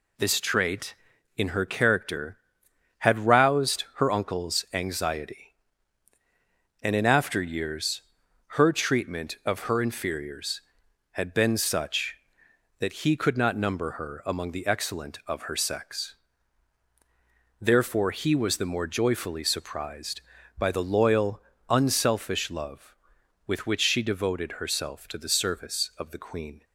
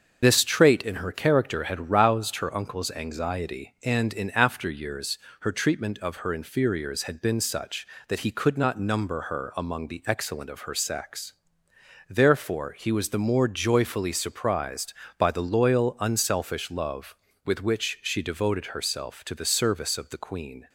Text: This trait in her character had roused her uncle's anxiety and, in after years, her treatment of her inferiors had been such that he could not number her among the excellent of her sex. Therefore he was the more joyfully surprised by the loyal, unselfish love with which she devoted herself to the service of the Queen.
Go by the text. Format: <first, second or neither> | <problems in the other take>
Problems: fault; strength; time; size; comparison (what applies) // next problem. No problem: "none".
first | loses the start of "This"; at 0.2 s; 60 ms // starts louder than the rest; until 1.2 s; 6.5 dB